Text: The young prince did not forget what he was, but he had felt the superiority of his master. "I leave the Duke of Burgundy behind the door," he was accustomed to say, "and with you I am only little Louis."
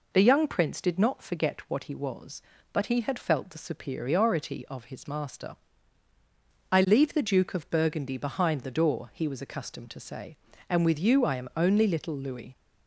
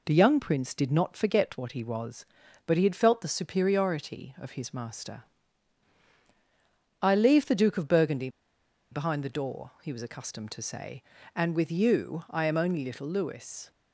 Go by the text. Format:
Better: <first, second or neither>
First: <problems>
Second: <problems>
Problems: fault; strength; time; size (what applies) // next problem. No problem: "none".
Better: first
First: none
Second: pauses between "Burgundy" and "behind"; noticeable; at 8.2 s; 0.63 s long